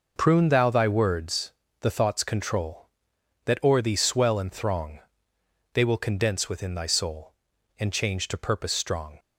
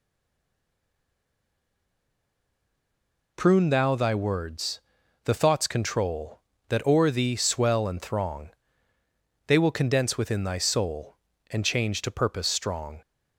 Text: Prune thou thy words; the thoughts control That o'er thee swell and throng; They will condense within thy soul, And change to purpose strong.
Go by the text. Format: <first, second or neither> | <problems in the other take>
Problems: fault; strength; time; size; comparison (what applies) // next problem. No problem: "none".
first | stays silent before the first word; strong; until 3.3 s; 3.3 s long